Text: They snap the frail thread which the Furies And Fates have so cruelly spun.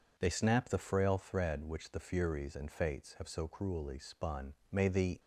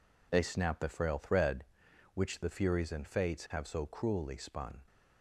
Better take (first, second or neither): second